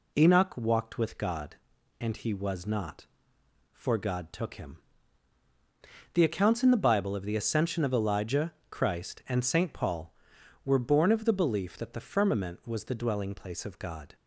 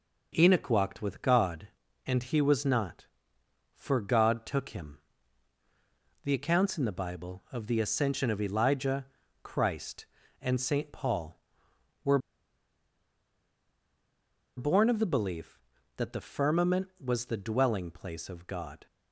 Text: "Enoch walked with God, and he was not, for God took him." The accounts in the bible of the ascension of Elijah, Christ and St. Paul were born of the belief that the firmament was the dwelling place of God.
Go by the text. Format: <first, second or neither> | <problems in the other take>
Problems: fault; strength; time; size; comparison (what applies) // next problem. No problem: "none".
first | pauses between "were" and "born"; strong; at 12.1 s; 2.3 s long